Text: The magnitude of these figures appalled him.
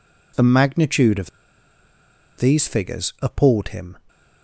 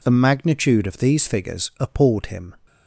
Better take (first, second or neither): second